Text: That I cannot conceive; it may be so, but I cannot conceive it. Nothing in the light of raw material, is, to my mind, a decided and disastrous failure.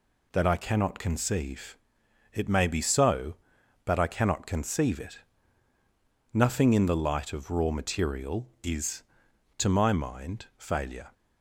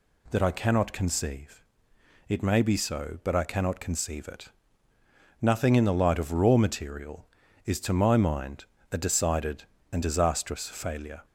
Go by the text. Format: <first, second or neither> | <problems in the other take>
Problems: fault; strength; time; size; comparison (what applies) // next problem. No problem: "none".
second | skips "a decided and disastrous"; at 10.5 s